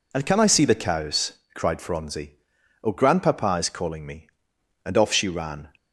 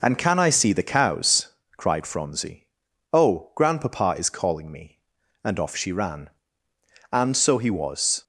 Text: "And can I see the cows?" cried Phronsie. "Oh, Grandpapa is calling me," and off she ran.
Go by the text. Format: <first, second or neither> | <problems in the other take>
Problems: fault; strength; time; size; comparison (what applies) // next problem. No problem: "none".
first | goes on to say "And so he was"; noticeable; from 7.1 s on; 1.1 s long